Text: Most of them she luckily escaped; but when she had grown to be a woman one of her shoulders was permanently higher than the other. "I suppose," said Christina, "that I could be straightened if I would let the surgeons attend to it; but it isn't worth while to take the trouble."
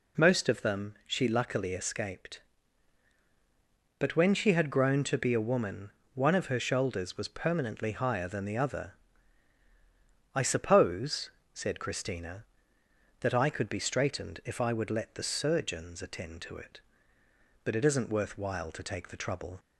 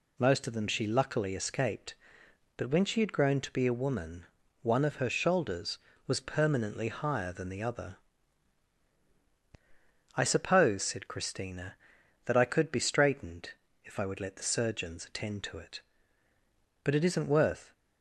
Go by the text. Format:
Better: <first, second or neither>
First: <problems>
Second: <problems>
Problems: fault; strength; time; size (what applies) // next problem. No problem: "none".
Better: first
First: pauses between "woman" and "one"; slight; at 5.9 s; 0.22 s long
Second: pauses between "woman" and "one"; slight; at 4.2 s; 0.34 s long // pauses between "straightened" and "if"; slight; at 13.5 s; 0.30 s long // stops before "while to take the trouble"; at 17.7 s